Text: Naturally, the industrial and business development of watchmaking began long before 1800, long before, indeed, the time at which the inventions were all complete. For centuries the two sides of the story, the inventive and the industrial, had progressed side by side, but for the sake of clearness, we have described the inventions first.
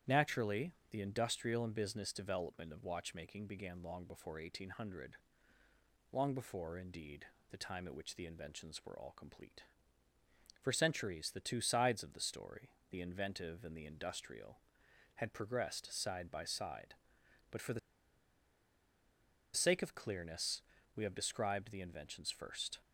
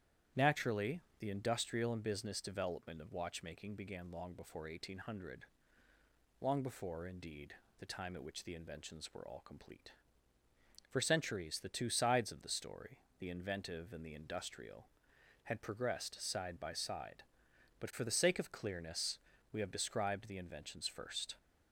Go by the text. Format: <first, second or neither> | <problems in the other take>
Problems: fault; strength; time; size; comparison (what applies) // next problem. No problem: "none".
second | starts louder than the rest; strong; until 1.2 s; 10.5 dB; strong in the second // pauses between "the" and "sake"; strong; at 17.7 s; 1.7 s long